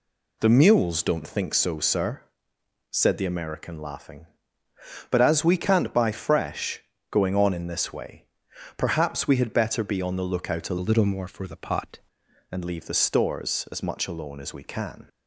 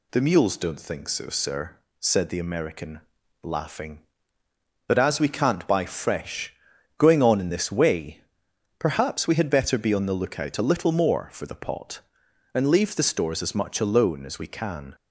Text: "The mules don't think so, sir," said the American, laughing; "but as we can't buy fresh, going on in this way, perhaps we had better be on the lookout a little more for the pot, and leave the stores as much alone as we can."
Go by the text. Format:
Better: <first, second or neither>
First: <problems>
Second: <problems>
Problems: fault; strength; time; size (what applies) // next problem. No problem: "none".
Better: second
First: changes voice from "little" to "pot"; from 10.8 to 11.9 s; 1.1 s long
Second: none